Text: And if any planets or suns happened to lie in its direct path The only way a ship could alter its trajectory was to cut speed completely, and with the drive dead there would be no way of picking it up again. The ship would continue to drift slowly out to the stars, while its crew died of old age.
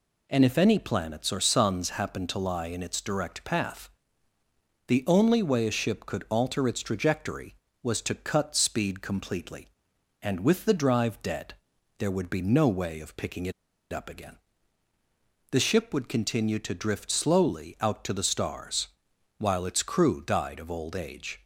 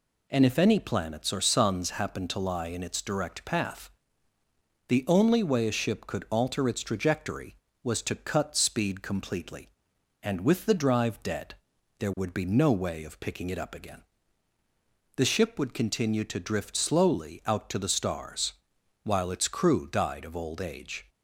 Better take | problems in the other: second | pauses between "path" and "The"; noticeable; at 3.8 s; 0.98 s long; noticeable in the second // pauses between "dead" and "there"; noticeable; at 11.5 s; 0.46 s long; noticeable in the second // pauses between "it" and "up"; at 13.5 s; 0.41 s long

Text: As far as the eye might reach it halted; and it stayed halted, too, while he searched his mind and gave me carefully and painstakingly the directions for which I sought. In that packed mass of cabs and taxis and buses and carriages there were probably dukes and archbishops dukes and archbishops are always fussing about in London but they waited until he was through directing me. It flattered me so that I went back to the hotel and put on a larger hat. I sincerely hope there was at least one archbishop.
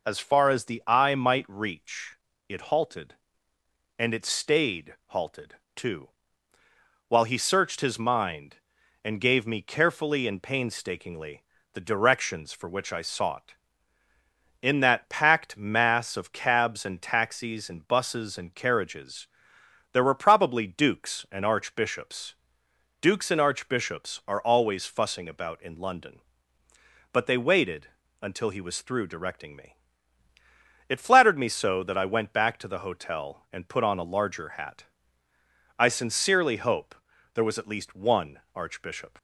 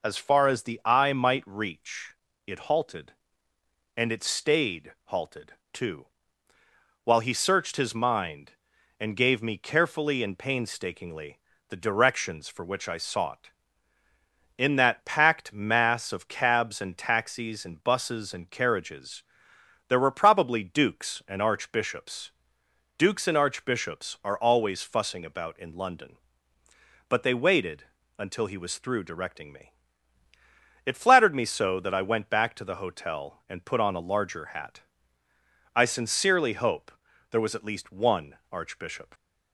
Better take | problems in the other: neither | pauses between "reach" and "it"; slight; the same in both // pauses between "painstakingly" and "the"; slight; the same in both // pauses between "carriages" and "there"; noticeable; the same in both // pauses between "archbishops" and "dukes"; noticeable; the same in both // pauses between "waited" and "until"; slight; the same in both // pauses between "hope" and "there"; the same in both

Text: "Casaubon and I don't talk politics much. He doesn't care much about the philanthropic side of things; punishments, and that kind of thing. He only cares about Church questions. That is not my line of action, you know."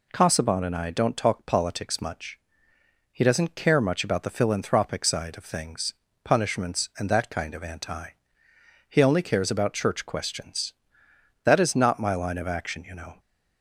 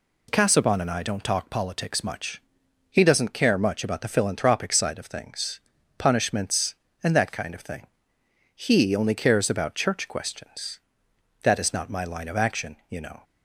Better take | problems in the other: second | says "anti" for "thing"; at 7.6 s

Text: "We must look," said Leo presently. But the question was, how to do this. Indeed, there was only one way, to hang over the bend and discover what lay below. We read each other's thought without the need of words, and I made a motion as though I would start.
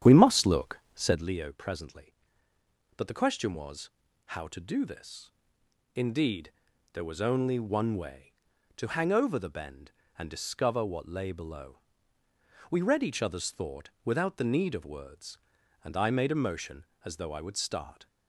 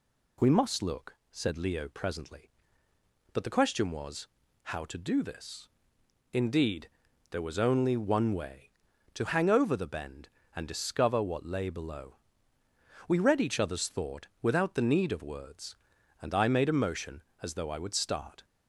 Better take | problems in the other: second | starts louder than the rest; strong; until 1.3 s; 10 dB

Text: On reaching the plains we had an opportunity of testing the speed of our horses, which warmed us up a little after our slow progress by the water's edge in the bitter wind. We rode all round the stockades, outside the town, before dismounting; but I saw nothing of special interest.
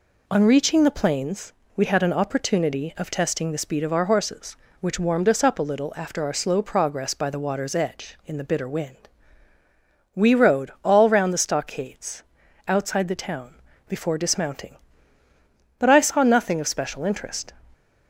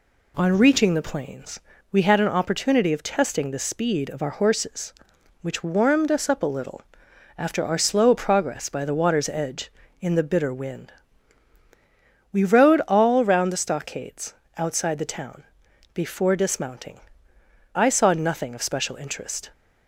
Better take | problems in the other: first | pauses between "plains" and "we"; slight; at 1.6 s; 0.32 s long; slight in the first // pauses between "little" and "after"; noticeable; at 6.8 s; 0.56 s long // skips "but"; at 17.3 s

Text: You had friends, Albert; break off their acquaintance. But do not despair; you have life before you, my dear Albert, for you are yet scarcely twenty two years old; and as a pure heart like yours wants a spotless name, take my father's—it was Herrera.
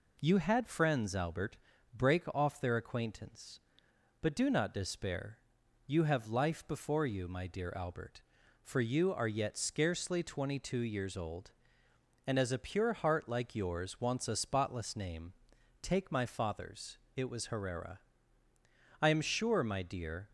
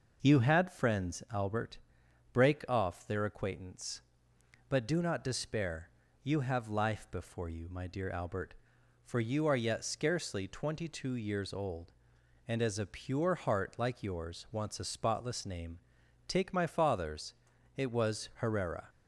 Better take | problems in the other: second | goes on to say "I am sure my dear"; noticeable; from 19.0 s on; 1.2 s long

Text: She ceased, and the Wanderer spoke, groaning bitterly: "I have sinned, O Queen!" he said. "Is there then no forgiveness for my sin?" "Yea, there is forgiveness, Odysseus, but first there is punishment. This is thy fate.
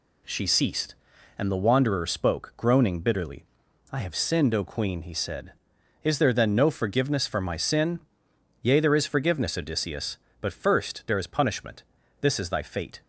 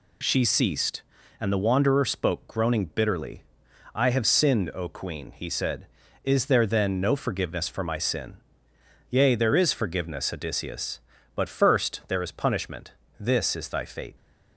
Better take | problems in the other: neither | none

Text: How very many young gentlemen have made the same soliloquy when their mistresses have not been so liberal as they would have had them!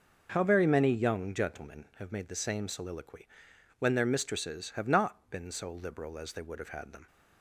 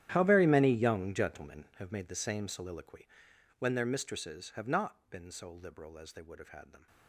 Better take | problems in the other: first | gets quieter; strong; throughout; 19 dB // pauses between "soliloquy" and "when"; noticeable; at 3.0 s; 0.54 s long; noticeable in the first

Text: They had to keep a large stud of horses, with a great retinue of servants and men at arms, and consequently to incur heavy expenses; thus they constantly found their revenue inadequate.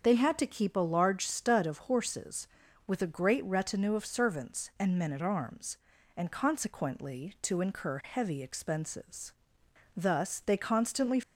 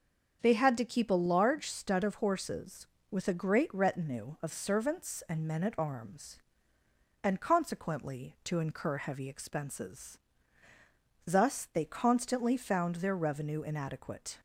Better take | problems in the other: second | starts louder than the rest; until 1.0 s; 6.5 dB; also in the second // stops before "found their revenue inadequate"; at 11.2 s

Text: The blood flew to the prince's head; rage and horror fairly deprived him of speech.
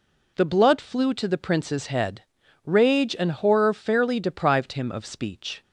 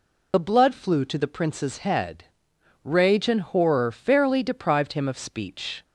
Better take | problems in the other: first | loses the start of "The"; at 0.3 s; 40 ms

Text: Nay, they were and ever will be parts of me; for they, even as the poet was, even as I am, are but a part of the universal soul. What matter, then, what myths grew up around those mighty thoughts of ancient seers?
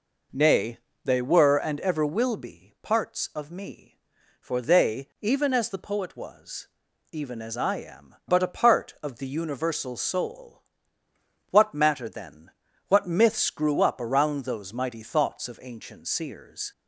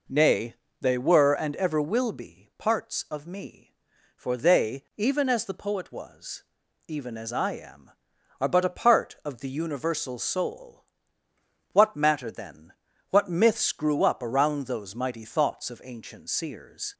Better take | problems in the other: second | skips "are"; at 8.2 s

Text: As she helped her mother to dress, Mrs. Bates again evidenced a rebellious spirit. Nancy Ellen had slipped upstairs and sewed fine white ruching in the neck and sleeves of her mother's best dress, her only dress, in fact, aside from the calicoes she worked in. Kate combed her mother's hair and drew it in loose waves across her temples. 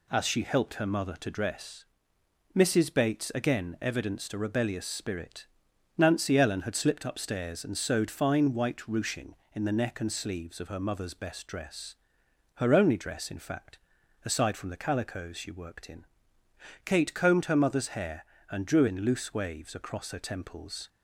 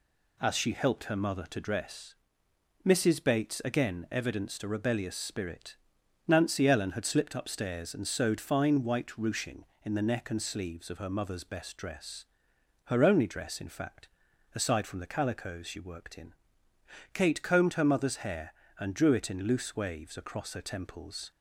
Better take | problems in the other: second | skips "it"; at 18.8 s

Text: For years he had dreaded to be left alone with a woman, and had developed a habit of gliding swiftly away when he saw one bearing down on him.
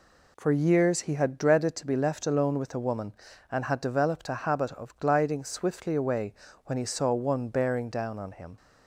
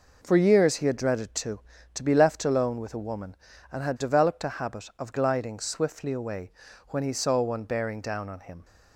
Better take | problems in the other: first | says "to" twice; at 1.9 s // pauses between "away" and "when"; at 6.5 s; 0.38 s long; slight in the first

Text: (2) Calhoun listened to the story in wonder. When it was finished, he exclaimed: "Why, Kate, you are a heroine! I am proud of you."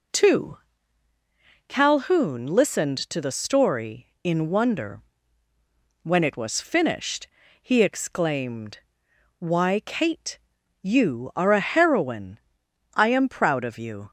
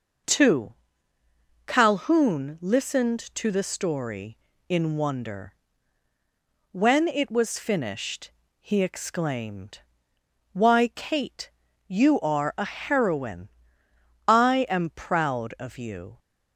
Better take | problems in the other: neither | none

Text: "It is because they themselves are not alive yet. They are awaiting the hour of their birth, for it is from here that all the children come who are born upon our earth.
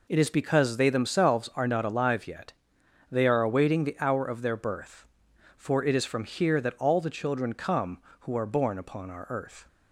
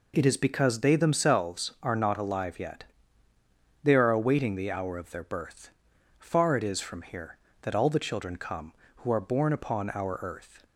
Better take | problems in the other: first | says "far" for "for"; at 6.2 s

